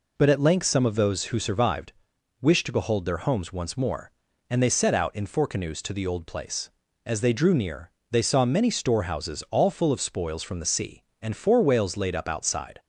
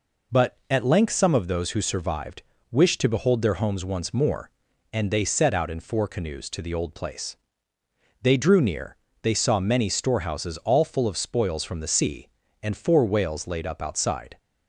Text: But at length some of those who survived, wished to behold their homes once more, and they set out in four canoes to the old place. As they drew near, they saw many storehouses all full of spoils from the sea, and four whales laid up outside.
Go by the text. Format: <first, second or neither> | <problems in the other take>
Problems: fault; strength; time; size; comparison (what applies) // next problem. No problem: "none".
first | skips "As"; at 7.7 s